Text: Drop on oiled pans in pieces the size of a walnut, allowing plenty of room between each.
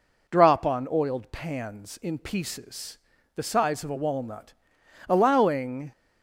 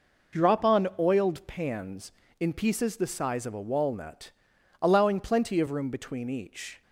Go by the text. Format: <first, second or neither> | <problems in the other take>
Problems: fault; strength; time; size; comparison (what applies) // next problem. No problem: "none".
second | pauses between "pieces" and "the"; at 2.9 s; 0.38 s long // stops before "plenty of room between each"; at 5.9 s